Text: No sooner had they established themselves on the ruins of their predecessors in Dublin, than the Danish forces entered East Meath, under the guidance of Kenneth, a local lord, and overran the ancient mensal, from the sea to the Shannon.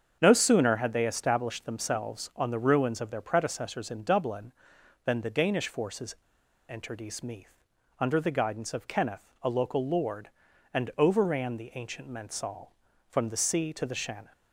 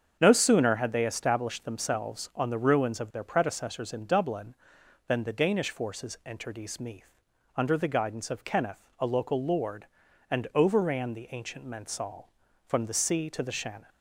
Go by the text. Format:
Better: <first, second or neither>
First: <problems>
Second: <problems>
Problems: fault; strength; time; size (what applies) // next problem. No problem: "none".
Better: second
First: starts louder than the rest; strong; until 1.2 s; 7.5 dB // pauses between "forces" and "entered"; noticeable; at 6.1 s; 0.52 s long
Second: starts louder than the rest; strong; until 1.2 s; 7.5 dB